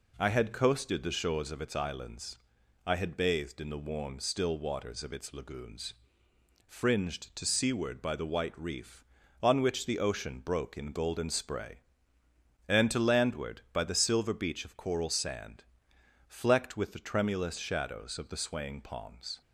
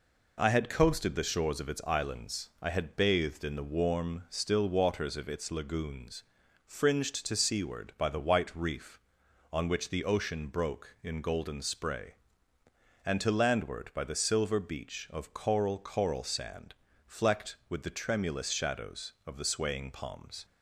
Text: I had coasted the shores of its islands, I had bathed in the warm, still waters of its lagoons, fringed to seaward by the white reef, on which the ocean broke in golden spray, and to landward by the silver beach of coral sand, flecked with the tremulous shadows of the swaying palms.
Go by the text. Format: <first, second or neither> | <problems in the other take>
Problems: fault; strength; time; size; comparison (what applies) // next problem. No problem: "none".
first | says "coral" twice; at 15.7 s